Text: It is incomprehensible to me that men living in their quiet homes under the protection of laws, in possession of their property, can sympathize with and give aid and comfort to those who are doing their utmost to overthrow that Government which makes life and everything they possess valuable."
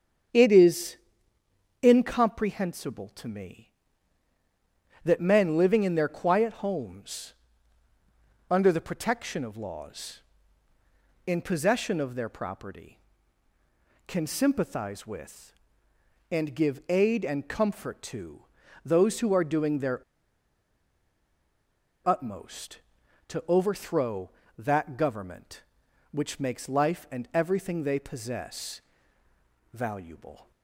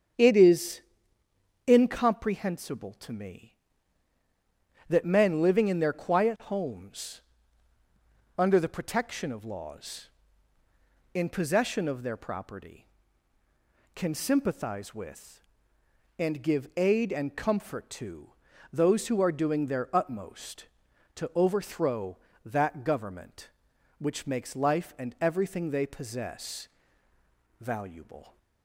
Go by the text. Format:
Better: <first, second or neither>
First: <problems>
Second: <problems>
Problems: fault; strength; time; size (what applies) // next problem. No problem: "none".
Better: second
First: starts louder than the rest; strong; until 2.1 s; 7.5 dB // pauses between "is" and "incomprehensible"; noticeable; at 0.9 s; 0.86 s long // pauses between "homes" and "under"; at 7.3 s; 1.1 s long // pauses between "to" and "those"; at 18.4 s; 0.42 s long // pauses between "their" and "utmost"; strong; at 20.0 s; 2.0 s long // pauses between "possess" and "valuable"; noticeable; at 28.8 s; 0.92 s long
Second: starts louder than the rest; strong; until 2.0 s; 7.5 dB // pauses between "is" and "incomprehensible"; noticeable; at 0.8 s; 0.86 s long // pauses between "homes" and "under"; at 7.2 s; 1.1 s long // pauses between "to" and "those"; at 18.2 s; 0.42 s long // pauses between "possess" and "valuable"; noticeable; at 26.6 s; 0.92 s long